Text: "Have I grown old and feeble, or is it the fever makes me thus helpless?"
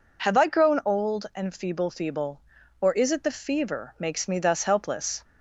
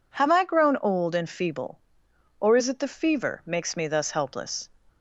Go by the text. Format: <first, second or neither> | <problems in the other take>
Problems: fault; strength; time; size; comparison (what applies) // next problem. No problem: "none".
second | says "feeble" twice; at 1.8 s